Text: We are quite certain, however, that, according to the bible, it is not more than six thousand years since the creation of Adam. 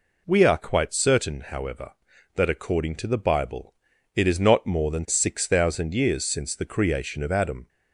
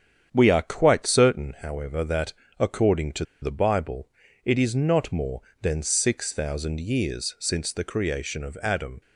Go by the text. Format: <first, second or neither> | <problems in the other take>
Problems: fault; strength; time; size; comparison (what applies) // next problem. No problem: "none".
first | starts louder than the rest; strong; until 1.3 s; 8.5 dB // pauses between "to" and "the"; slight; at 3.2 s; 0.18 s long